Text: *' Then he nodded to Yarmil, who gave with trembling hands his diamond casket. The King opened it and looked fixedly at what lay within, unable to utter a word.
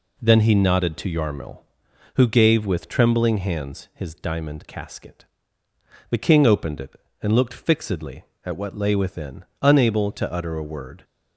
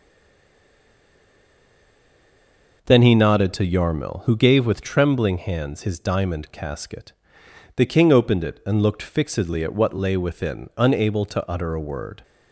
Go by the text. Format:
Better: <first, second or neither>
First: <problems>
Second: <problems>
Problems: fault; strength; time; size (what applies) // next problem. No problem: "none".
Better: first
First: none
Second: stays silent before the first word; strong; until 2.8 s; 2.8 s long